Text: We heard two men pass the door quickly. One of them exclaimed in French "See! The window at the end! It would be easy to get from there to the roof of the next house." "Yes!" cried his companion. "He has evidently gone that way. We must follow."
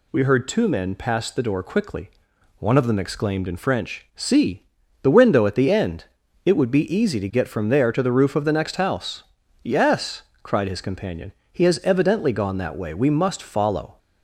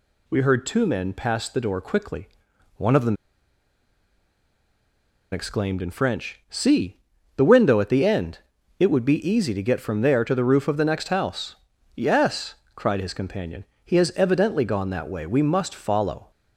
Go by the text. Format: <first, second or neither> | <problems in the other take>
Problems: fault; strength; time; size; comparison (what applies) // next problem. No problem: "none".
first | pauses between "them" and "exclaimed"; strong; at 3.1 s; 2.1 s long